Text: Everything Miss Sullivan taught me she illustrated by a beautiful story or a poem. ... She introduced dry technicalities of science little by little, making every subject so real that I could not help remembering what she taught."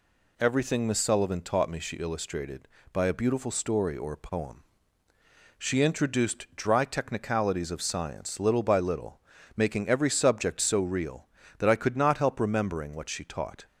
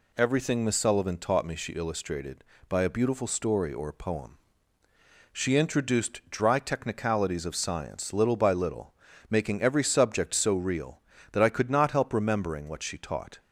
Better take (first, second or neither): neither